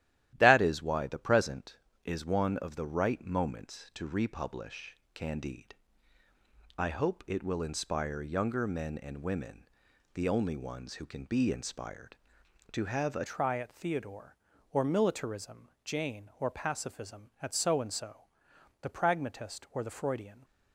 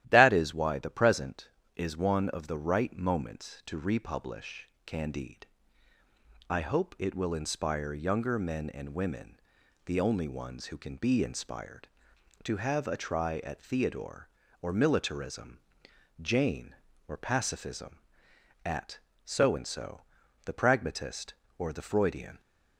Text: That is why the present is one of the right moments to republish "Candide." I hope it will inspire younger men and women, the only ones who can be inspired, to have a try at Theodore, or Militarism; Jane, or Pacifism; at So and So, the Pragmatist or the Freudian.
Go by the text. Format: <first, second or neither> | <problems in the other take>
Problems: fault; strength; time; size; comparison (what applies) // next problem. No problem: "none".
second | starts louder than the rest; strong; until 1.3 s; 13 dB; strong in the second // pauses between "republish" and "Candide"; slight; at 4.9 s; 0.18 s long; slight in the second // changes voice at "try"; from 13.2 s on; 7.2 s long